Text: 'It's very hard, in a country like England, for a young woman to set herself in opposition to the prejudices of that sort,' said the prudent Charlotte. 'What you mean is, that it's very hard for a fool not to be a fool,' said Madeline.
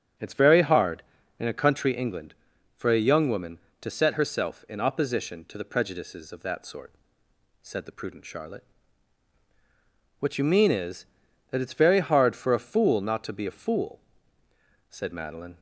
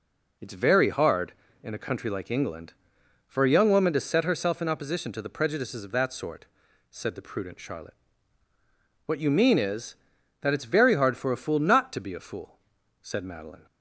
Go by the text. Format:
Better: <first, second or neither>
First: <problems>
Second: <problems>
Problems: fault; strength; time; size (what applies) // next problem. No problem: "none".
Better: second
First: starts louder than the rest; strong; until 1.5 s; 7.5 dB // skips "like"; at 1.9 s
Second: none